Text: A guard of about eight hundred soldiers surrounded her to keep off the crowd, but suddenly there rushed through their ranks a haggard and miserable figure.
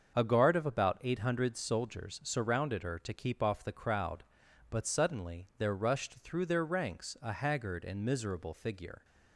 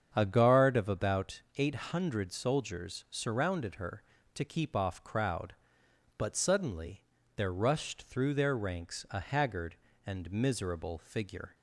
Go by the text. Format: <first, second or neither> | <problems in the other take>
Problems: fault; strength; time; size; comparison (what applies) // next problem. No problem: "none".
first | starts louder than the rest; strong; until 1.1 s; 7.5 dB; also in the first // pauses between "about" and "eight"; slight; at 1.4 s; 0.16 s long // skips "the"; at 5.0 s // pauses between "suddenly" and "there"; slight; at 7.0 s; 0.36 s long